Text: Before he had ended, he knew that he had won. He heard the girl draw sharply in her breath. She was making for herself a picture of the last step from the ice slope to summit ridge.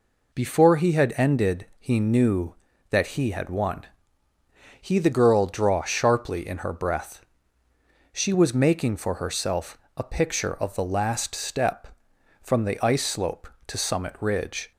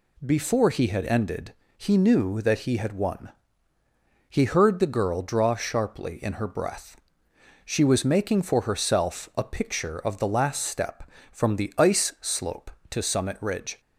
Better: second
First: skips "heard"; at 4.9 s // pauses between "herself" and "a"; slight; at 9.7 s; 0.20 s long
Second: none

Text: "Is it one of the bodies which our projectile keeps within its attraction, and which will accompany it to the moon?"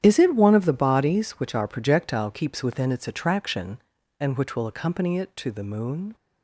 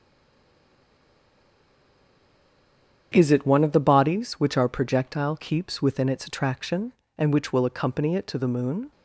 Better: first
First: starts louder than the rest; strong; until 1.0 s; 10 dB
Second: stays silent before the first word; strong; until 3.1 s; 3.1 s long // starts louder than the rest; strong; until 4.1 s; 9 dB

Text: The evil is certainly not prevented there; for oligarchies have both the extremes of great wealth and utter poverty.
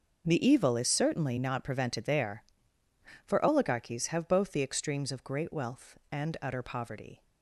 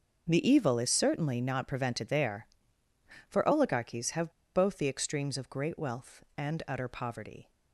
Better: first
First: starts louder than the rest; until 1.3 s; 6 dB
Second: starts louder than the rest; until 1.3 s; 6 dB // pauses between "have" and "both"; slight; at 4.2 s; 0.24 s long

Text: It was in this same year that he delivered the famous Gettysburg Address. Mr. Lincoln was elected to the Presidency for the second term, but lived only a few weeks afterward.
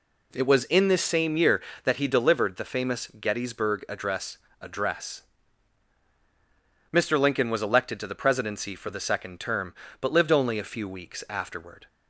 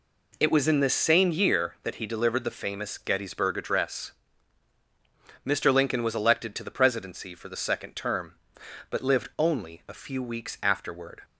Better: second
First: says "Address" twice; at 4.6 s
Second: none

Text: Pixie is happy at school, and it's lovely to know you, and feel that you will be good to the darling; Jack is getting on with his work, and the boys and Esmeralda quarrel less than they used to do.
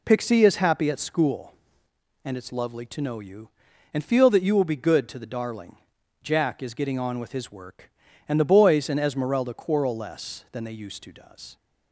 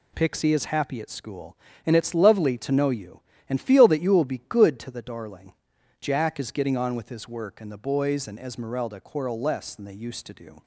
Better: second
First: says "does" for "do"; at 11.1 s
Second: none

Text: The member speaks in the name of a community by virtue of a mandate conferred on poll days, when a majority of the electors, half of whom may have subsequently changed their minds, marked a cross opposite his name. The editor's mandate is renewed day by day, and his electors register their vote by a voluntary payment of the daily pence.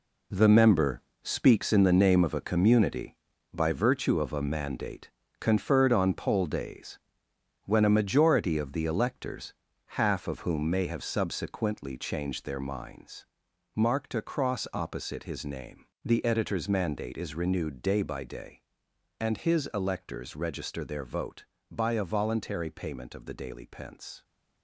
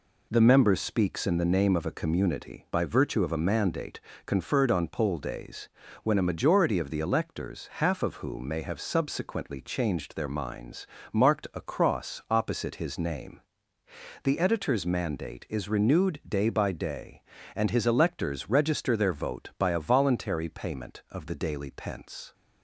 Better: second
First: gets quieter; strong; throughout; 9.5 dB // pauses between "member" and "speaks"; slight; at 1.0 s; 0.22 s long // pauses between "mandate" and "conferred"; slight; at 5.0 s; 0.30 s long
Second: pauses between "mandate" and "conferred"; slight; at 3.9 s; 0.26 s long

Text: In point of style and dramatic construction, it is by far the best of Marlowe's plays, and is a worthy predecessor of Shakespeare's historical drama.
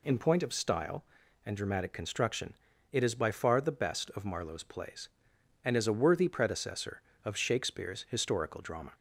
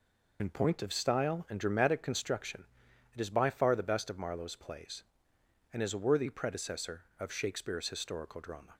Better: first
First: none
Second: loses the start of "In"; at 0.3 s; 50 ms

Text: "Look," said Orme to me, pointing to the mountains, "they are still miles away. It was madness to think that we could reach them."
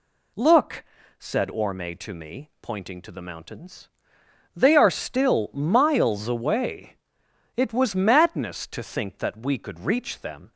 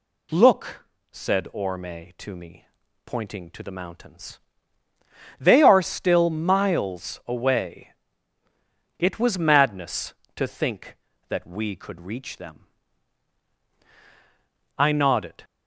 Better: first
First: none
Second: goes on to say "I nodded"; noticeable; from 14.7 s on; 0.68 s long

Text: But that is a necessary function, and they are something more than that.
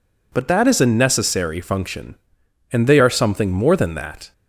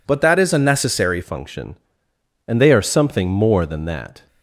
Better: first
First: none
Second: changes voice at "function"; from 1.2 s on; 3.0 s long

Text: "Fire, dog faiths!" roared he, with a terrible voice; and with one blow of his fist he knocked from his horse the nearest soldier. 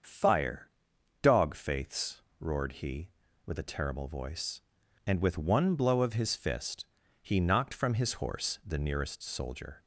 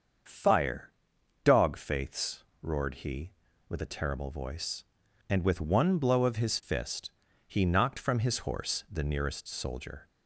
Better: neither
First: starts louder than the rest; until 1.5 s; 7 dB // pauses between "fist" and "he"; at 6.8 s; 0.38 s long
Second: starts louder than the rest; until 1.8 s; 7 dB // pauses between "fist" and "he"; at 7.0 s; 0.38 s long

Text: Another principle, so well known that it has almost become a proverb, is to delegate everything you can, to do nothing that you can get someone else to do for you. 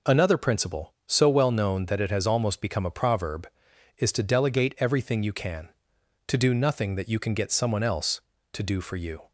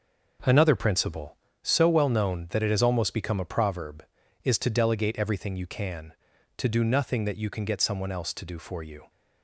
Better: first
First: none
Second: gets quieter; strong; throughout; 8.5 dB

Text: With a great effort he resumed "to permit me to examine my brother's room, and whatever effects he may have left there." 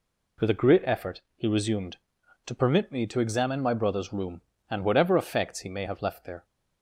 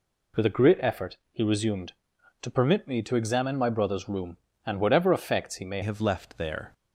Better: first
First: pauses between "effort" and "he"; slight; at 1.1 s; 0.16 s long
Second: pauses between "effort" and "he"; slight; at 1.1 s; 0.16 s long // changes voice at "have"; from 5.8 s on; 0.9 s long

